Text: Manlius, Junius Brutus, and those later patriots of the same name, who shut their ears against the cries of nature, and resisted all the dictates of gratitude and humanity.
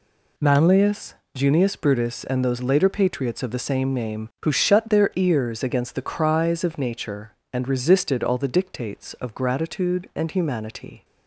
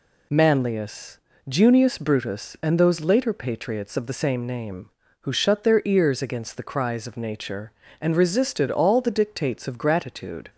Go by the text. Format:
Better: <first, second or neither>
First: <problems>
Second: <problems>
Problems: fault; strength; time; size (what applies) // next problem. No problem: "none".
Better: first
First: none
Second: stops before "and humanity"; at 10.4 s